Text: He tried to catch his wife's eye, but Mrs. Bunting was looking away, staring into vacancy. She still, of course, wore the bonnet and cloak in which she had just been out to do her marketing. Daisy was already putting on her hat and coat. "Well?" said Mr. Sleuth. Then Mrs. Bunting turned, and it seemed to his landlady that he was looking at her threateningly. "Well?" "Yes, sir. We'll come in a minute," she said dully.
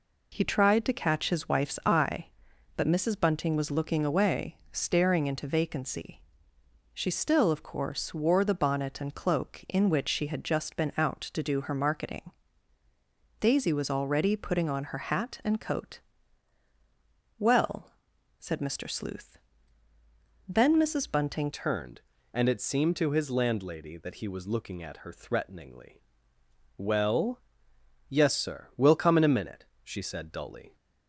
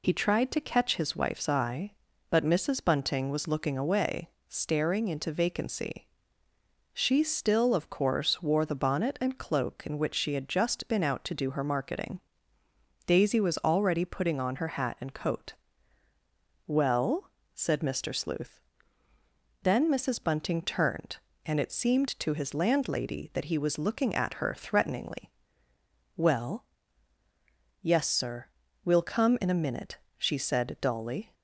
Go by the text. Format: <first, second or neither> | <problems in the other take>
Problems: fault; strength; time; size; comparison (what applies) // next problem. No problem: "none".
second | changes voice at "turned"; from 21.5 s on; 9.2 s long